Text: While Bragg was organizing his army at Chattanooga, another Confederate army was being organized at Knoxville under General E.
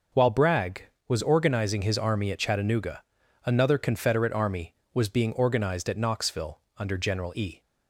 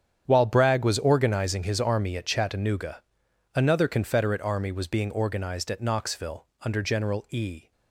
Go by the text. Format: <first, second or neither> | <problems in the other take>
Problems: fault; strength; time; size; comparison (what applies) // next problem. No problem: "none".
first | gets quieter; strong; throughout; 13.5 dB // pauses between "Knoxville" and "under"; slight; at 6.4 s; 0.16 s long; slight in the first